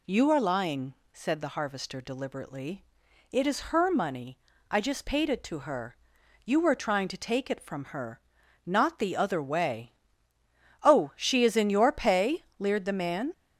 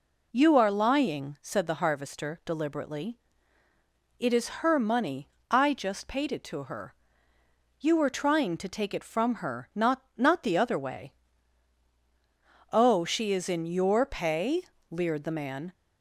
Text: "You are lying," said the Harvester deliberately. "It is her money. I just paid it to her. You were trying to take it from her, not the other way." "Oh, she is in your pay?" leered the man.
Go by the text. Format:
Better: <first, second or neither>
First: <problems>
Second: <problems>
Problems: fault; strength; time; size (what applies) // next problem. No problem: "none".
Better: first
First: none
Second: says "not" twice; at 10.1 s